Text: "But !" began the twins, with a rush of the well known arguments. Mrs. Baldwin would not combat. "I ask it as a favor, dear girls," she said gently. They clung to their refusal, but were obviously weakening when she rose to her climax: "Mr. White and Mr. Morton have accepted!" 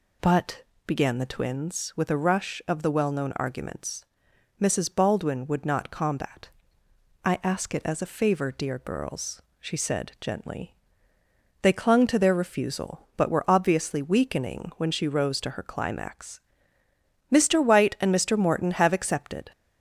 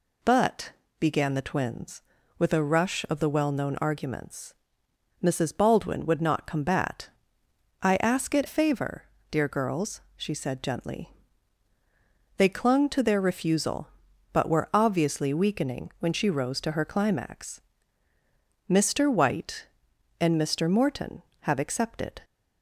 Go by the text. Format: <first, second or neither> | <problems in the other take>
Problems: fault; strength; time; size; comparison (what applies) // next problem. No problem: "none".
first | skips "as a"; at 8.4 s